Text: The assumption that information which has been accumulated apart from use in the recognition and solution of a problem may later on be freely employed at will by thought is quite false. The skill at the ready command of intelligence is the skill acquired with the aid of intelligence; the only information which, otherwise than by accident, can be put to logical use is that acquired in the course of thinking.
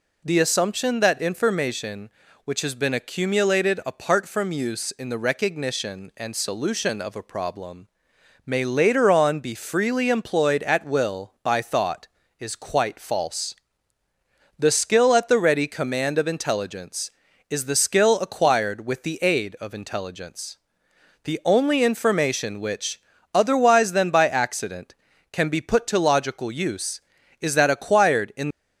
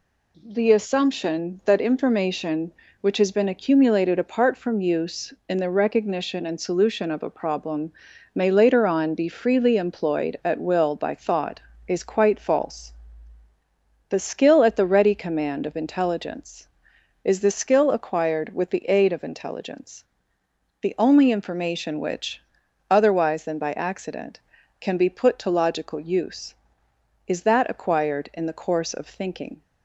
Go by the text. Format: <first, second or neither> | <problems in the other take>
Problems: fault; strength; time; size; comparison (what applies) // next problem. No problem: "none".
second | pauses between "problem" and "may"; noticeable; at 7.8 s; 0.60 s long; also in the second // stops before "the course of thinking"; at 28.5 s